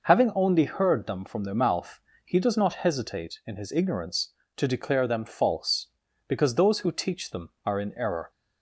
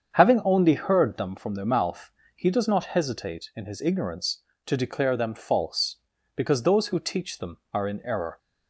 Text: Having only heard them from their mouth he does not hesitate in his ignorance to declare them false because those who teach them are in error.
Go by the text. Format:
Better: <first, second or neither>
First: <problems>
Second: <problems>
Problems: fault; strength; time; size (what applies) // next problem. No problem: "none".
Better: first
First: pauses between "mouth" and "he"; slight; at 2.0 s; 0.24 s long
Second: starts louder than the rest; strong; until 1.4 s; 7.5 dB // pauses between "mouth" and "he"; slight; at 2.1 s; 0.24 s long